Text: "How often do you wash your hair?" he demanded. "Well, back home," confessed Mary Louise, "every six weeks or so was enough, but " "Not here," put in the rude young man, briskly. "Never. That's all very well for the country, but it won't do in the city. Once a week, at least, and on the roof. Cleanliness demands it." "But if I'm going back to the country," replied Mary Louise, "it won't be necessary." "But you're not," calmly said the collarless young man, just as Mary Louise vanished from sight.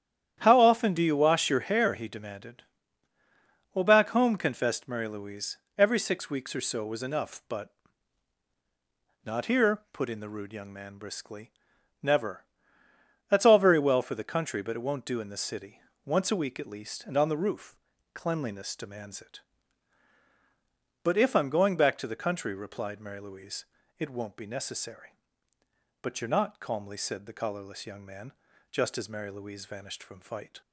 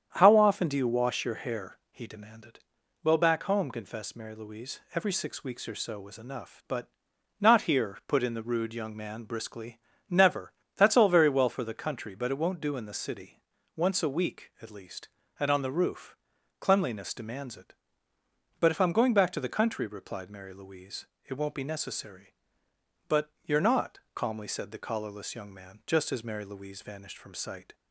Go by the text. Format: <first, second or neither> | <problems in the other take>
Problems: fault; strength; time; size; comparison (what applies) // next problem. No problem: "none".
second | starts louder than the rest; strong; until 1.4 s; 10.5 dB; strong in the second // says "fight" for "sight"; at 30.1 s